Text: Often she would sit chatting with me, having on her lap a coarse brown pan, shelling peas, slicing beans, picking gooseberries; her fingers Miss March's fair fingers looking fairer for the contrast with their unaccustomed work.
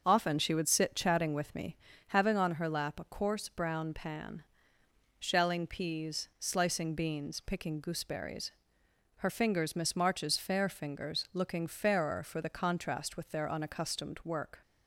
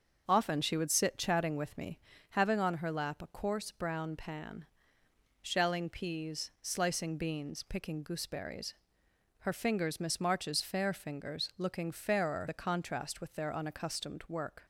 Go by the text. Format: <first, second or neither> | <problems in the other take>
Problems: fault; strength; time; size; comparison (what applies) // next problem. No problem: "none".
first | starts louder than the rest; until 1.2 s; 6.5 dB; also in the first // skips "for"; at 12.4 s